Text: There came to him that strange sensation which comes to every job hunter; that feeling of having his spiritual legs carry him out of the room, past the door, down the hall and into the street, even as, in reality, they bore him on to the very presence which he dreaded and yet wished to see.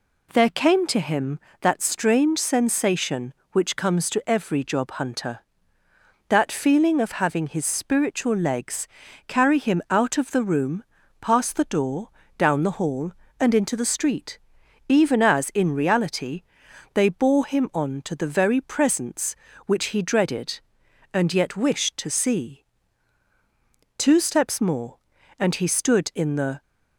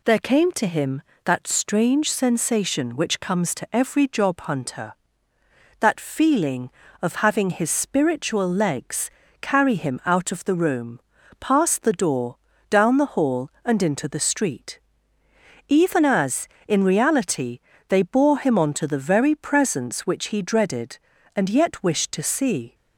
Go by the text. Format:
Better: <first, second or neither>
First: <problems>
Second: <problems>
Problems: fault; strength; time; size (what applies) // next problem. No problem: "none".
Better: second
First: pauses between "legs" and "carry"; at 8.8 s; 0.40 s long // goes on to say "Two steps more and he stood in the"; strong; from 23.9 s on; 2.6 s long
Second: pauses between "legs" and "carry"; slight; at 9.1 s; 0.30 s long